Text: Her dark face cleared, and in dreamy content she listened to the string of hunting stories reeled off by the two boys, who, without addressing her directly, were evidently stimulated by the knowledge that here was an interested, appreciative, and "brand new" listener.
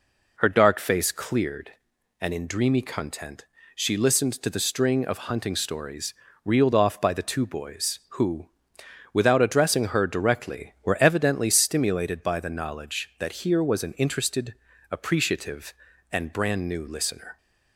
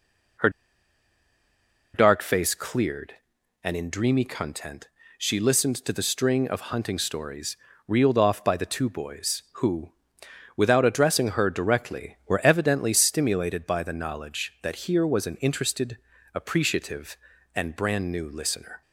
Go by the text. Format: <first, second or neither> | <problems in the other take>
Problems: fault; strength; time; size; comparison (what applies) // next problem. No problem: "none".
first | pauses between "Her" and "dark"; strong; at 0.4 s; 1.4 s long // pauses between "content" and "she"; slight; at 4.8 s; 0.28 s long; slight in the first // pauses between "stories" and "reeled"; slight; at 7.5 s; 0.32 s long; slight in the first